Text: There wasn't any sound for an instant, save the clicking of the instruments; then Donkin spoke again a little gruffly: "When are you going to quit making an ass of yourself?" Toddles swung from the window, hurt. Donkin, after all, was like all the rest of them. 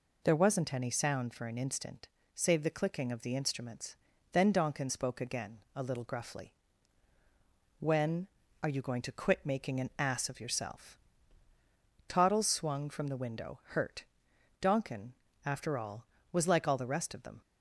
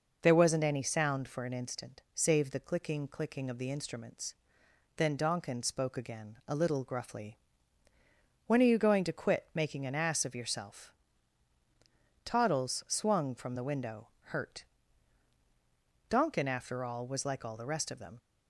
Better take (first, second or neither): first